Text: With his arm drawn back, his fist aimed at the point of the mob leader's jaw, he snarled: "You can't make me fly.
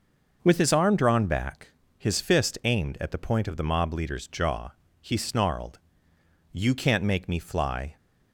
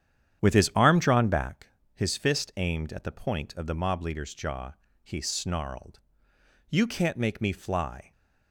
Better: first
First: none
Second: starts louder than the rest; strong; until 1.6 s; 9.5 dB

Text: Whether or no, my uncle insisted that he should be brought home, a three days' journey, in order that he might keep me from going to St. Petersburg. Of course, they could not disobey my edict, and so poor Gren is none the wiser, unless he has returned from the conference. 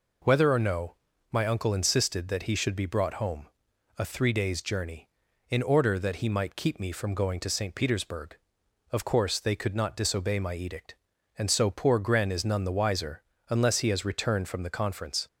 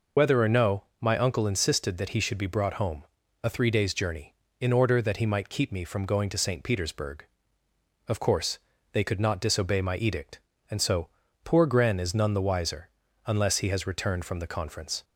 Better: first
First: none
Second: loses the start of "Whether"; at 0.1 s; 70 ms // pauses between "so" and "poor"; slight; at 11.0 s; 0.36 s long

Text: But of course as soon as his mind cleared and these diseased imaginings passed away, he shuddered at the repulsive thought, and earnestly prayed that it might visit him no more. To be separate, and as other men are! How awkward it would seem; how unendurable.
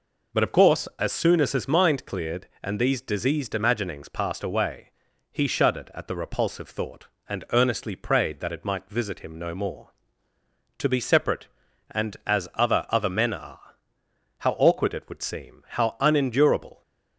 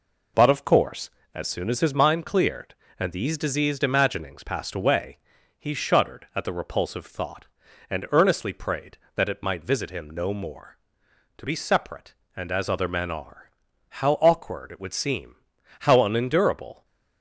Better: second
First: says "other" twice; at 12.8 s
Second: none

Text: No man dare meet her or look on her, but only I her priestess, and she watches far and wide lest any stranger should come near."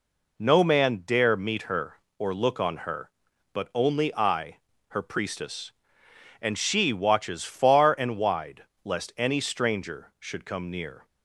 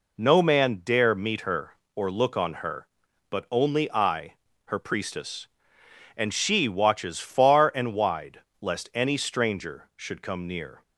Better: neither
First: pauses between "I" and "her"; slight; at 4.5 s; 0.32 s long // pauses between "wide" and "lest"; slight; at 8.6 s; 0.20 s long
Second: pauses between "I" and "her"; slight; at 4.3 s; 0.32 s long // pauses between "wide" and "lest"; slight; at 8.4 s; 0.20 s long

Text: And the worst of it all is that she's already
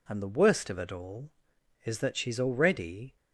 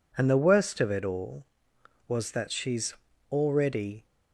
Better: first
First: none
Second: says "was" for "is"; at 2.0 s // pauses between "she's" and "already"; slight; at 2.9 s; 0.36 s long

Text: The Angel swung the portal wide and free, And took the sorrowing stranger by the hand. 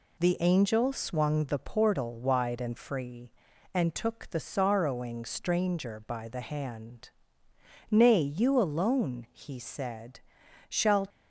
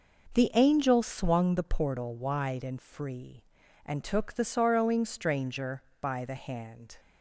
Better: second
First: goes on to say "Nay you alone he said shall"; strong; from 7.8 s on; 3.1 s long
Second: none

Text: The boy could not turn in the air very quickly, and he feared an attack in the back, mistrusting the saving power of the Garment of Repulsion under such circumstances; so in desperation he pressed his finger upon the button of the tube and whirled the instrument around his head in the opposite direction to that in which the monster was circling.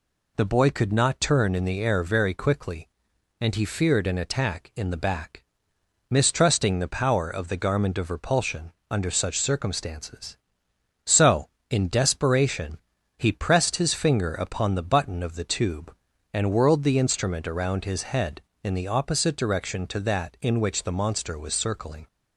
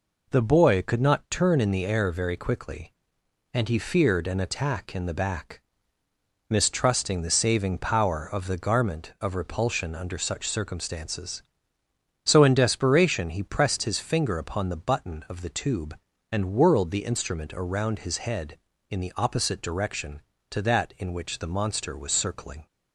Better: second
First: skips "saving"; at 6.8 s // pauses between "Repulsion" and "under"; slight; at 8.7 s; 0.18 s long // pauses between "desperation" and "he"; at 12.7 s; 0.38 s long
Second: none

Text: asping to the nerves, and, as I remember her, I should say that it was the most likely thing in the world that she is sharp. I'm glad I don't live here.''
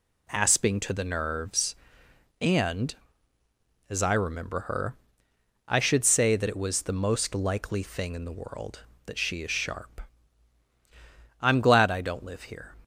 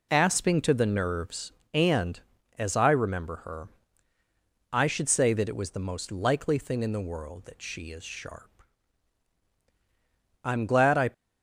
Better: first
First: none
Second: stops before "don't live here"; at 11.1 s

